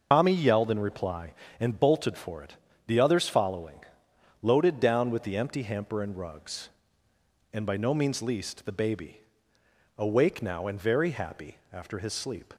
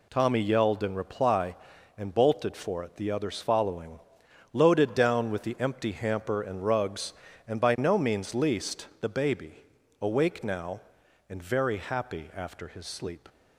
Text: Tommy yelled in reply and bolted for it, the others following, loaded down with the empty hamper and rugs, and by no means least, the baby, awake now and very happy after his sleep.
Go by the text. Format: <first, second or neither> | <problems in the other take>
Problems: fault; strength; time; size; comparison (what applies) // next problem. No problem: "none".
second | loses the start of "Tommy"; at 0.1 s; 120 ms